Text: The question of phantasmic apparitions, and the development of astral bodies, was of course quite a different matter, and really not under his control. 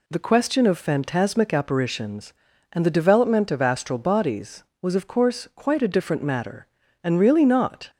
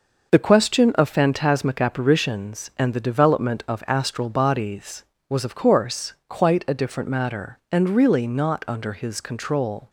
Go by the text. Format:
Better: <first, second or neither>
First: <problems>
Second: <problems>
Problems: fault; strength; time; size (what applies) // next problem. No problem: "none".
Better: second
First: stops before "under his control"; at 7.8 s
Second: none